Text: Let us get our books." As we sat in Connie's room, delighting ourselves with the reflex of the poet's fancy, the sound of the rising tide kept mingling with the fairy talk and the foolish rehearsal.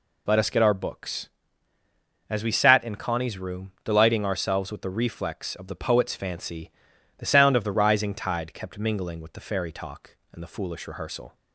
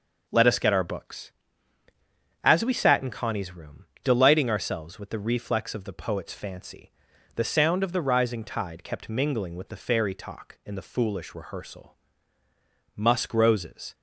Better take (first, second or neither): first